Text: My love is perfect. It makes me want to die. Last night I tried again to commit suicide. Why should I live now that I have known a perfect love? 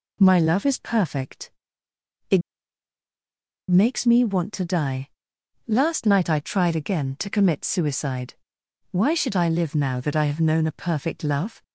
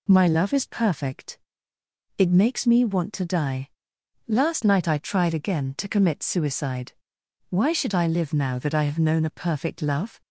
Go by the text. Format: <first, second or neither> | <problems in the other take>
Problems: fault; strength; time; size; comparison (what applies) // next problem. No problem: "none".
second | pauses between "It" and "makes"; strong; at 2.4 s; 1.2 s long